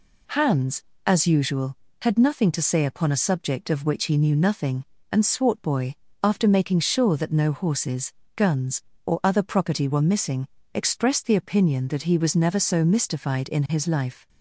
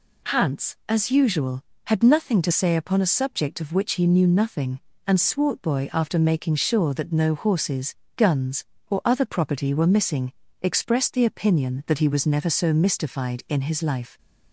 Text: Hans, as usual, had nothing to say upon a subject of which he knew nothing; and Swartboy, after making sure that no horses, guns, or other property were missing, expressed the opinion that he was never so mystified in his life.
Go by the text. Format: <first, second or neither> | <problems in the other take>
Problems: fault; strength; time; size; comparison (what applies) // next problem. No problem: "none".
neither | none